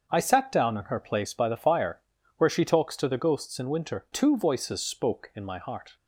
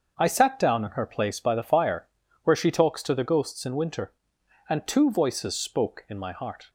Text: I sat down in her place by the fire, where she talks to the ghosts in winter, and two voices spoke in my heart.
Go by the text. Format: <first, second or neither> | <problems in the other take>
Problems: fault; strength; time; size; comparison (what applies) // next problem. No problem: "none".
second | starts louder than the rest; until 1.1 s; 6.5 dB; also in the second // skips "and"; at 4.0 s